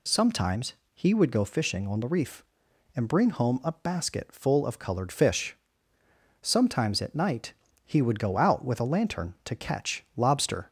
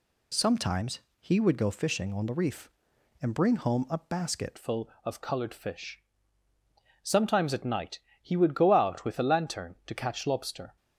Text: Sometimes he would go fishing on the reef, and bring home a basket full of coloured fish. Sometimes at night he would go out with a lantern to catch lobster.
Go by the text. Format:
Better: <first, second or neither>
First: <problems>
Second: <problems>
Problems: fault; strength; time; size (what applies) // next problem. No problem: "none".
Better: first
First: pauses between "Sometimes" and "he"; slight; at 0.7 s; 0.20 s long // pauses between "night" and "he"; slight; at 7.5 s; 0.32 s long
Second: pauses between "Sometimes" and "he"; slight; at 1.0 s; 0.20 s long // changes voice at "full"; from 4.5 s on; 6.2 s long // pauses between "night" and "he"; slight; at 7.9 s; 0.24 s long